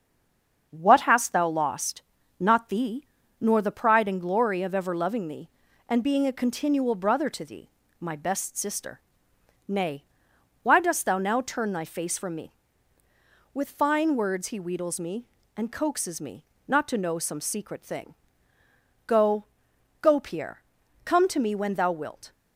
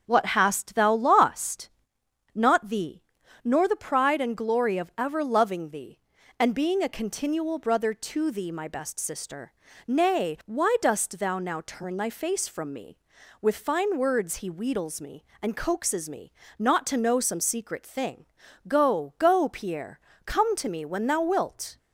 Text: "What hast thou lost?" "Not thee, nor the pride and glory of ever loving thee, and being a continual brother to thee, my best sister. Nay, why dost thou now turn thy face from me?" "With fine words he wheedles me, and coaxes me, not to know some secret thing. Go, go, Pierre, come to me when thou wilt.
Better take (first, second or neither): second